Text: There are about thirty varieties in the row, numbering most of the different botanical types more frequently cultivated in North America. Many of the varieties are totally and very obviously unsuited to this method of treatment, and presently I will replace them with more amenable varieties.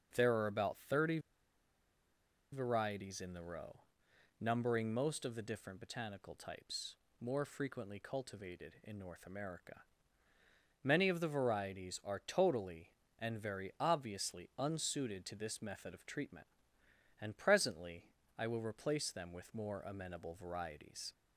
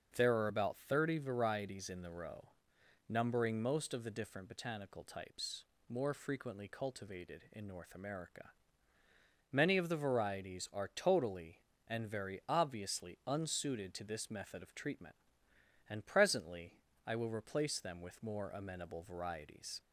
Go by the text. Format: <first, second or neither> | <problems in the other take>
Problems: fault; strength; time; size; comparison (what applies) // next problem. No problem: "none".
second | starts louder than the rest; noticeable; until 1.1 s; 6 dB; noticeable in the second // pauses between "thirty" and "varieties"; strong; at 1.1 s; 1.3 s long // pauses between "types" and "more"; slight; at 6.9 s; 0.26 s long; slight in the second // pauses between "presently" and "I"; slight; at 18.0 s; 0.34 s long; slight in the second